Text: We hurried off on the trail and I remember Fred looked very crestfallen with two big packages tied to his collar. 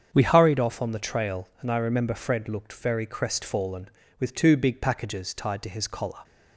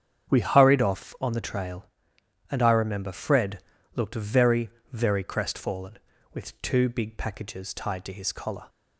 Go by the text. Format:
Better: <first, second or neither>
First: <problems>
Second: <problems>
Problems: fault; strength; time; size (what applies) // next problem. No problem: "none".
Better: first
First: starts louder than the rest; strong; until 1.1 s; 7.5 dB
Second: starts louder than the rest; strong; until 1.3 s; 8 dB // pauses between "Fred" and "looked"; slight; at 3.6 s; 0.34 s long // says "very" twice; at 4.9 s